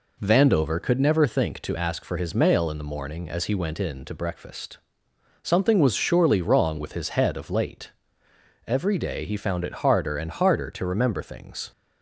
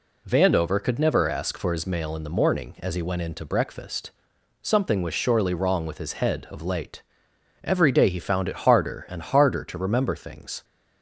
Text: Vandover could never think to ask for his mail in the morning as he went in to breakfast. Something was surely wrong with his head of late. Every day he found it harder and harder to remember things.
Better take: first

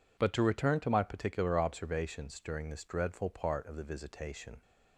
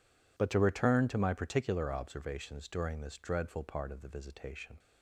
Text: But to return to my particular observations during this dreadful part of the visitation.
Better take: neither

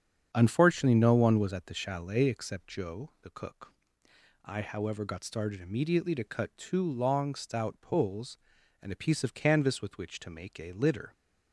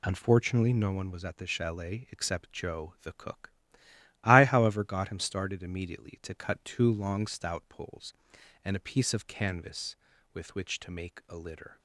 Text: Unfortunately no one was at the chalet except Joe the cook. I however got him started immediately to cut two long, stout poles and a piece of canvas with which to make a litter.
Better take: second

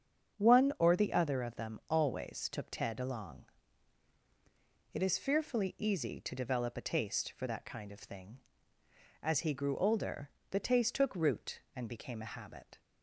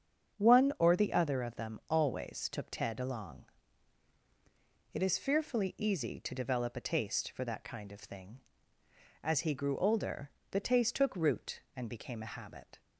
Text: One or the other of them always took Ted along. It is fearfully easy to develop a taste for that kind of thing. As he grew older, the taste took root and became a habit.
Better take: neither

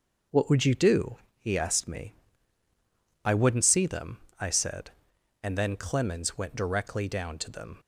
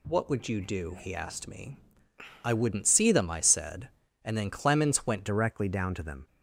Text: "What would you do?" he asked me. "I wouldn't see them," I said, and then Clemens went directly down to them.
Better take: first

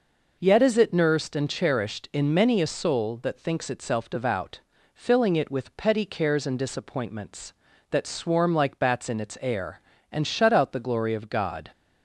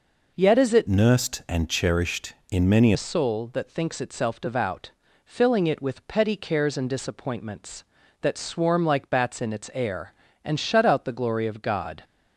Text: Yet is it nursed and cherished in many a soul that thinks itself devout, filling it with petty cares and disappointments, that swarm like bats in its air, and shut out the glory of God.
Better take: first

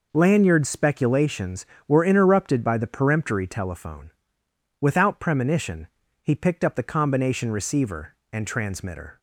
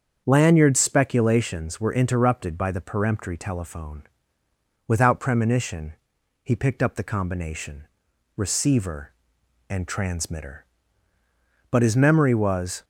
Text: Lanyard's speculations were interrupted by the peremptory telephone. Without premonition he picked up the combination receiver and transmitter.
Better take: first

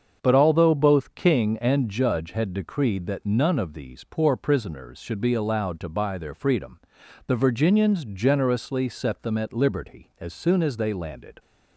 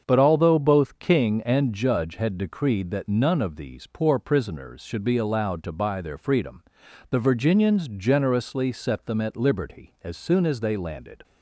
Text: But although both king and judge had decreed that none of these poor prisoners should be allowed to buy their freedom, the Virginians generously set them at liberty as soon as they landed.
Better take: neither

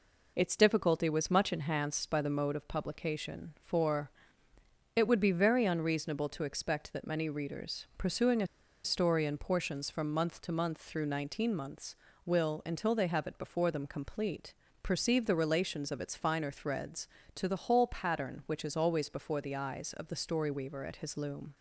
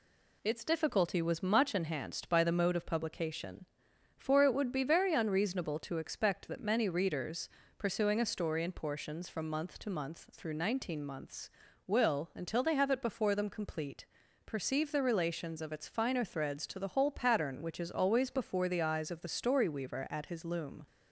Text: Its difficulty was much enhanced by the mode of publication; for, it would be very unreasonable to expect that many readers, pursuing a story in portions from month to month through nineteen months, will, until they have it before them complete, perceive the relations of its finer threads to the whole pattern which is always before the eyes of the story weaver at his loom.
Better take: second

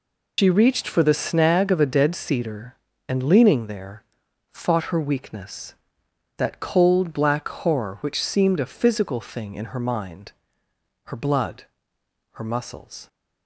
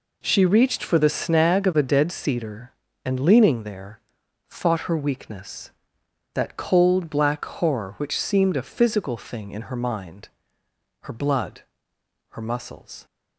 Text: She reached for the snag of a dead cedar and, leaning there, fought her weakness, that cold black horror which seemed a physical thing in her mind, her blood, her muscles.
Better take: second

